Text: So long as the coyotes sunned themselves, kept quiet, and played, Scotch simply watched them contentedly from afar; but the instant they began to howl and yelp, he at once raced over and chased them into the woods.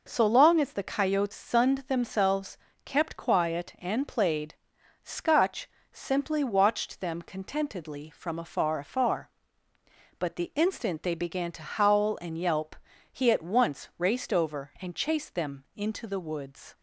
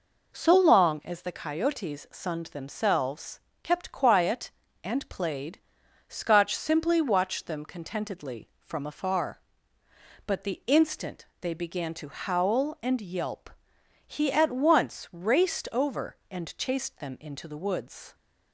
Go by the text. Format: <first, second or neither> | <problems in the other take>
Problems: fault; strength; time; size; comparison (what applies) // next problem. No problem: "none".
second | pauses between "Scotch" and "simply"; slight; at 5.6 s; 0.24 s long // says "afar" twice; at 8.7 s